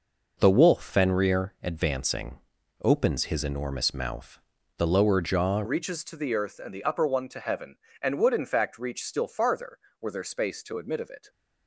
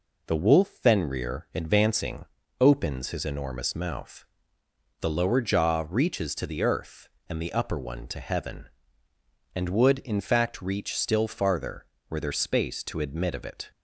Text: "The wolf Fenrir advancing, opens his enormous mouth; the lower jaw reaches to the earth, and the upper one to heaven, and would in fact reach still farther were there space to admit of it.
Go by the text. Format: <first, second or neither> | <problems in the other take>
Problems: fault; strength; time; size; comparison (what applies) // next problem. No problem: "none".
second | changes voice at "reaches"; from 5.6 s on; 5.6 s long